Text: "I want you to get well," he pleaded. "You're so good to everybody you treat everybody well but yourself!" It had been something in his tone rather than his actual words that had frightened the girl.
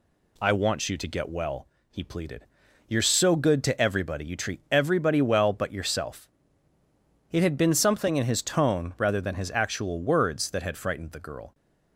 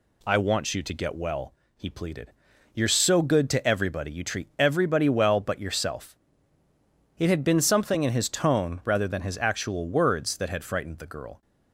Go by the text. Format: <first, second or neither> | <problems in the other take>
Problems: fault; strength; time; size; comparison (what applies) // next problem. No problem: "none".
neither | none